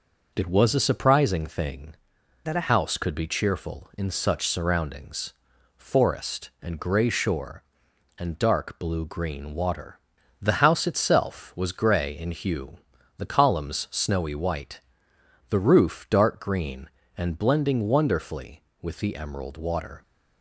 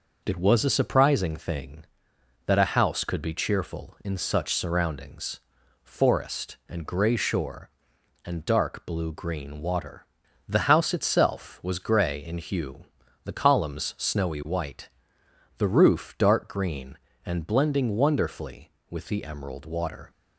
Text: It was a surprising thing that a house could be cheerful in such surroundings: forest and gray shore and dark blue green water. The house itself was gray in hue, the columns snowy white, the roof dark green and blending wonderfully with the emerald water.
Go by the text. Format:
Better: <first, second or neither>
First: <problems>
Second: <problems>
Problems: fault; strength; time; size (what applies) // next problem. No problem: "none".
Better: second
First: changes voice from "that" to "a"; from 2.4 to 2.7 s; 0.3 s long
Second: none